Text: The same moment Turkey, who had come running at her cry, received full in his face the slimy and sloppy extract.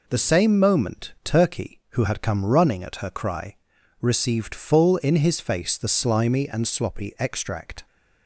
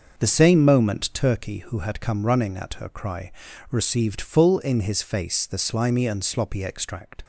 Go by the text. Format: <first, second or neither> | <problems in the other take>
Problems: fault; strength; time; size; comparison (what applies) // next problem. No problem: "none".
first | starts louder than the rest; until 1.4 s; 6 dB